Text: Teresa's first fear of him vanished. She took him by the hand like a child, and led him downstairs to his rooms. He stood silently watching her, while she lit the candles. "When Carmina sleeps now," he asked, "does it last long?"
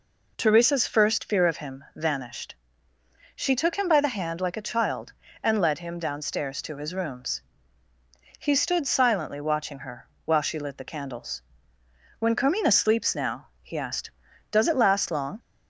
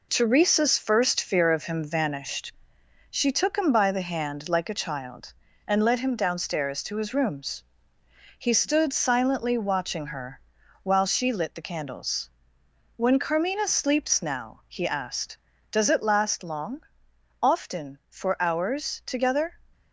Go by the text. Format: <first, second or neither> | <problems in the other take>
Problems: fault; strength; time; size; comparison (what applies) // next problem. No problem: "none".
first | goes on to say "Often for hours together"; strong; from 17.3 s on; 2.2 s long